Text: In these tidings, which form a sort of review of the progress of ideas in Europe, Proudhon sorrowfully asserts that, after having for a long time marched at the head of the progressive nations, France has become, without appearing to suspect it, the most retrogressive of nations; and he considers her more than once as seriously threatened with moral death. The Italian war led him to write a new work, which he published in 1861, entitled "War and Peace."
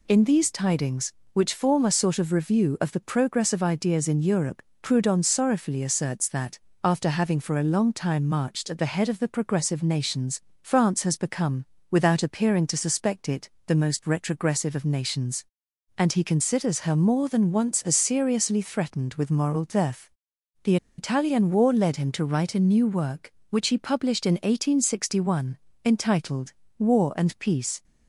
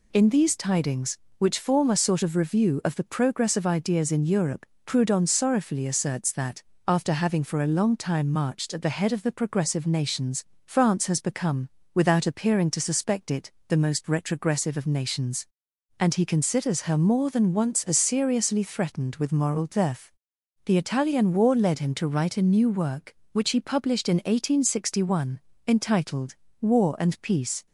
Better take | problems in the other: second | pauses between "The" and "Italian"; slight; at 20.7 s; 0.21 s long // pauses between "entitled" and "War"; slight; at 26.5 s; 0.26 s long; slight in the second

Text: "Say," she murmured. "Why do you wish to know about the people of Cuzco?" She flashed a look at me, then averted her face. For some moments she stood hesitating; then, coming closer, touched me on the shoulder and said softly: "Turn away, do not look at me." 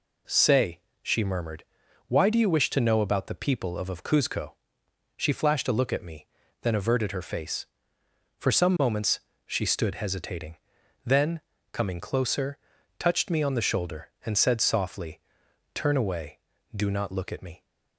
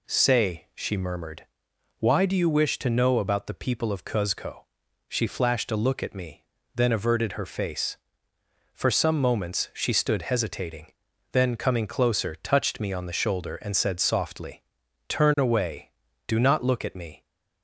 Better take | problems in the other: second | says "of" twice; at 3.8 s // pauses between "moments" and "she"; slight; at 9.2 s; 0.26 s long

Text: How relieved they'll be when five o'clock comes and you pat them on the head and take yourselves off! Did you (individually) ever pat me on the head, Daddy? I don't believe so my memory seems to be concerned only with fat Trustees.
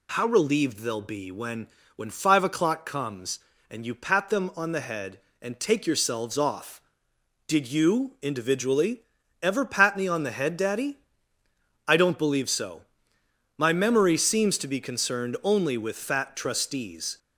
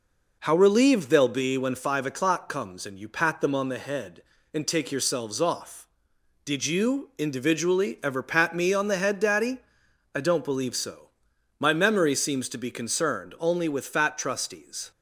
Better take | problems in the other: second | says "when" twice; at 1.9 s // pauses between "so" and "my"; noticeable; at 12.8 s; 0.76 s long; noticeable in the second

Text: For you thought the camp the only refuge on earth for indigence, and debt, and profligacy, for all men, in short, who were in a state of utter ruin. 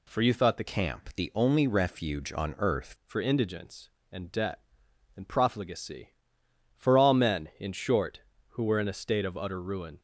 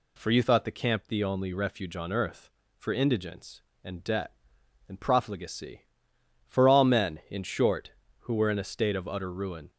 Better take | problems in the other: second | changes voice from "camp" to "earth"; from 0.6 to 2.9 s; 2.3 s long

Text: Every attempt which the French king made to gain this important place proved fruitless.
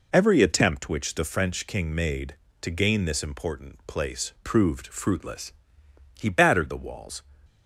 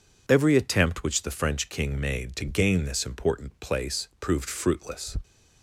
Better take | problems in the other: second | goes on to say "He battered the walls"; noticeable; from 6.1 s on; 1.0 s long

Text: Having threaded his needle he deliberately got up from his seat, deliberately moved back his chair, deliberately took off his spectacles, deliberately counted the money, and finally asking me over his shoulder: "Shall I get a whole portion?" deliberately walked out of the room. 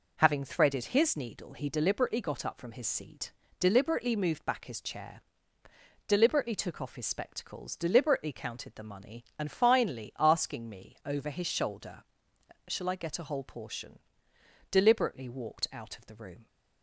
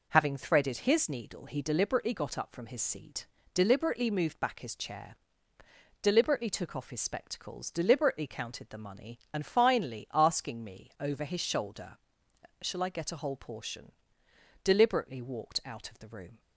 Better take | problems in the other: neither | none

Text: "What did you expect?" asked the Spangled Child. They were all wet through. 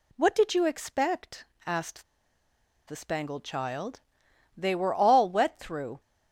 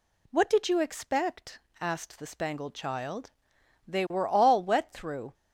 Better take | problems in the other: second | pauses between "asked" and "the"; noticeable; at 2.0 s; 0.84 s long

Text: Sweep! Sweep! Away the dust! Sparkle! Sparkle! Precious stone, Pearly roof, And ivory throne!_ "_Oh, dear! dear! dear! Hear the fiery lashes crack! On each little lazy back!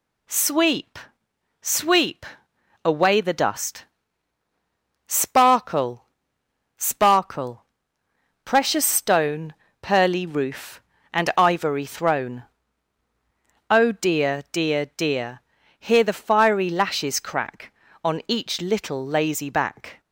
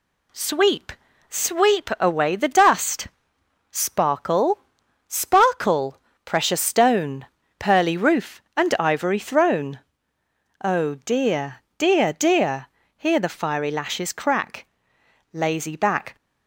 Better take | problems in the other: first | skips "On each little"; at 14.9 s

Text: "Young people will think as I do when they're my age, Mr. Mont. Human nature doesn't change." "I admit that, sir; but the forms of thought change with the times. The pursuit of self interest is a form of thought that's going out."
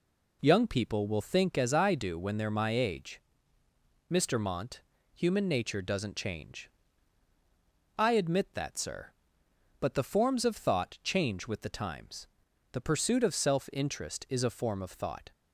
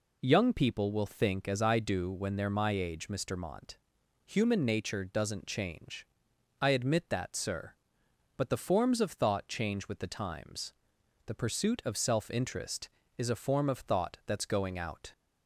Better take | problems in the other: second | stops before "that's going out"; at 15.3 s

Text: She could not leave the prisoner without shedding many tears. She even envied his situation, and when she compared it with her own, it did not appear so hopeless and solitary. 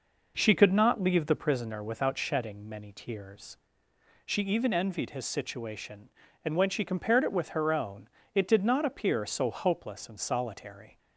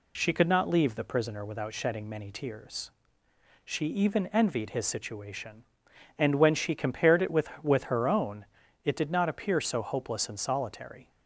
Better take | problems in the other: first | says "with" twice; at 7.6 s

